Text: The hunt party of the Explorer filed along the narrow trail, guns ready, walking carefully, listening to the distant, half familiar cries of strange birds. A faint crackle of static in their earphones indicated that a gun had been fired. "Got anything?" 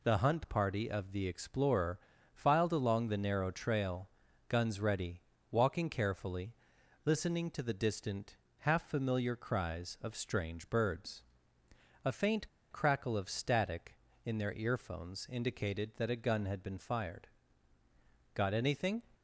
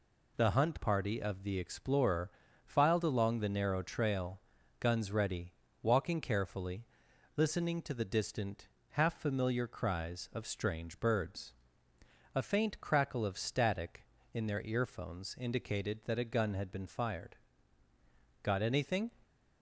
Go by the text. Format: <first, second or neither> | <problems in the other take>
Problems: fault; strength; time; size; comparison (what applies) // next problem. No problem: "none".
second | pauses between "Explorer" and "filed"; slight; at 1.9 s; 0.34 s long; slight in the second // pauses between "faint" and "crackle"; slight; at 12.4 s; 0.22 s long